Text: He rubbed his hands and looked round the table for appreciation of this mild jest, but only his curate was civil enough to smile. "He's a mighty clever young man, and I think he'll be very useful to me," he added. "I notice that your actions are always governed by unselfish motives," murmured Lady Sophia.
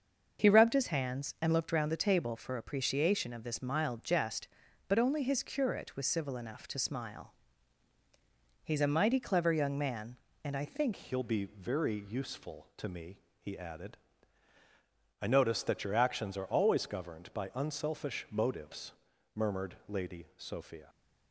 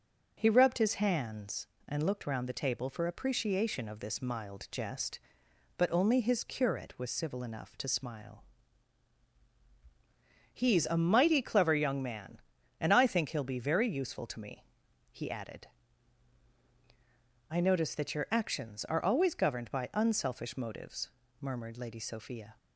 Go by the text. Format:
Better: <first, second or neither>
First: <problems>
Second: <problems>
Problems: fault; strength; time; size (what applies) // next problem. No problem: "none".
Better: second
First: starts louder than the rest; until 1.4 s; 6.5 dB // changes voice at "he'll"; from 10.9 s on; 9.9 s long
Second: none